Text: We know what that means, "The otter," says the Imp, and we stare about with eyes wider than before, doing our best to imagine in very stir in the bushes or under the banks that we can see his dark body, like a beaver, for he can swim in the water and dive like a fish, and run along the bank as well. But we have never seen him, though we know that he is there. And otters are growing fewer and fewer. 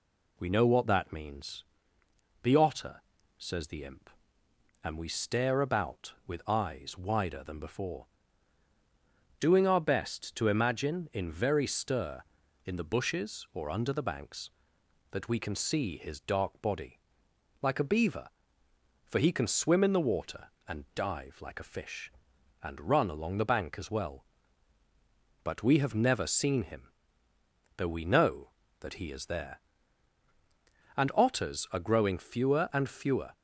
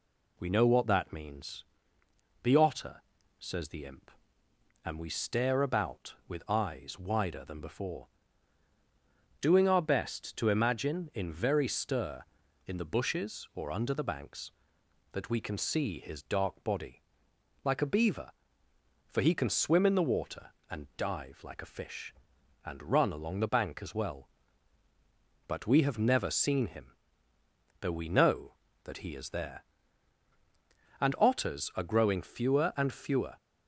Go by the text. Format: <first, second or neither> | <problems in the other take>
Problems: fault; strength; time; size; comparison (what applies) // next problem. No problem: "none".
neither | none